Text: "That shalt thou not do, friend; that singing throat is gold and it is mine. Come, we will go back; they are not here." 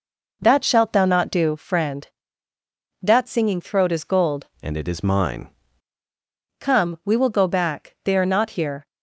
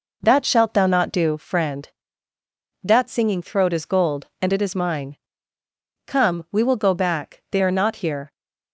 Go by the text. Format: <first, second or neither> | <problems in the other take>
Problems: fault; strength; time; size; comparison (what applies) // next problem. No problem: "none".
second | changes voice from "and" to "mine"; from 4.5 to 5.4 s; 0.9 s long